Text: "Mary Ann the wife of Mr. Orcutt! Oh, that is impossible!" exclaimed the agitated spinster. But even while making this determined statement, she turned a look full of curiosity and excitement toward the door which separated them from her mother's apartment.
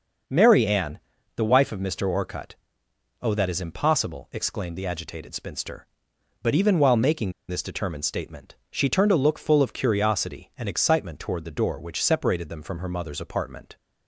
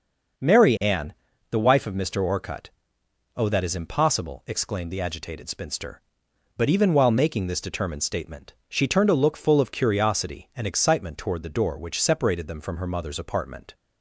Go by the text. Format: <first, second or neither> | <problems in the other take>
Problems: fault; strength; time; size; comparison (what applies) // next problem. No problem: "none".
second | pauses between "Ann" and "the"; slight; at 0.9 s; 0.36 s long; slight in the second // pauses between "making" and "this"; slight; at 7.3 s; 0.17 s long